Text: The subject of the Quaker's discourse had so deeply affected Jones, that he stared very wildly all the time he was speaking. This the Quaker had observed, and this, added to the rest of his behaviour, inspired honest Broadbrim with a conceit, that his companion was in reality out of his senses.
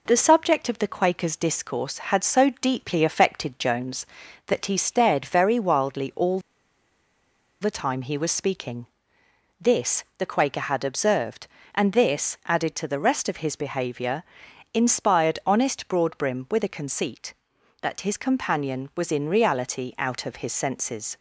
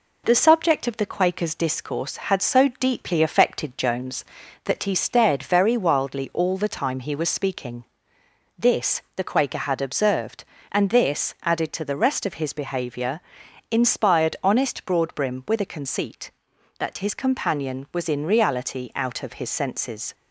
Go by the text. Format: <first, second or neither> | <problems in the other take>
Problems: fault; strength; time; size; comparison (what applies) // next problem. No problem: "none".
second | pauses between "all" and "the"; at 6.3 s; 1.2 s long